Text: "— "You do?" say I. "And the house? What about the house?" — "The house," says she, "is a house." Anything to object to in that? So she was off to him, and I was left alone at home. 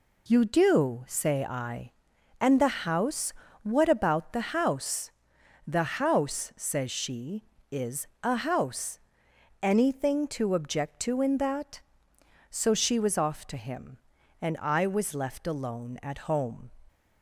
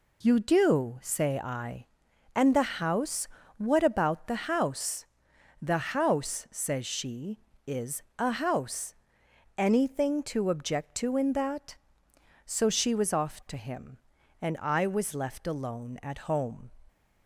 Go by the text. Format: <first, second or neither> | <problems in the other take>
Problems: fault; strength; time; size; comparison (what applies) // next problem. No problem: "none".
neither | pauses between "is" and "a"; slight; the same in both